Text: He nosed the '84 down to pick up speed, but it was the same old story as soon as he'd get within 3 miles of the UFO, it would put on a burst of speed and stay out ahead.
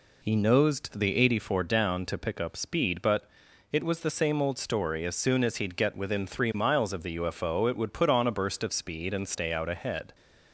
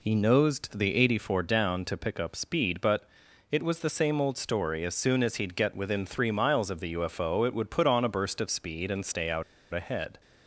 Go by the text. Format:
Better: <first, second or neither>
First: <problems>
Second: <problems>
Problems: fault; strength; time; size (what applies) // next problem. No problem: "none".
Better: first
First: pauses between "but" and "it"; noticeable; at 3.2 s; 0.48 s long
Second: pauses between "but" and "it"; noticeable; at 3.0 s; 0.48 s long // pauses between "out" and "ahead"; slight; at 9.4 s; 0.30 s long